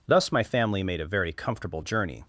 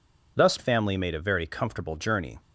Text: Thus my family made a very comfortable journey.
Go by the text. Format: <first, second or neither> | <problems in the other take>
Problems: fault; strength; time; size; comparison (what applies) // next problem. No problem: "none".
first | skips "my"; at 0.5 s